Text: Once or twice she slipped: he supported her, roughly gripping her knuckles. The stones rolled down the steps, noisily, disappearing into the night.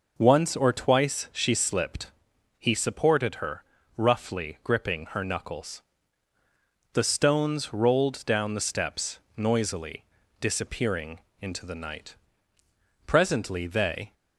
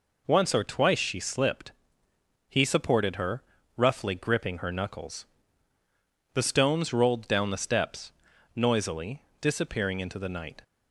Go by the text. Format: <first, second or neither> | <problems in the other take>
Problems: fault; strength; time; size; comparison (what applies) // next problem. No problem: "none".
second | pauses between "disappearing" and "into"; slight; at 11.1 s; 0.20 s long // goes on to say "Presently they"; noticeable; from 13.0 s on; 1.0 s long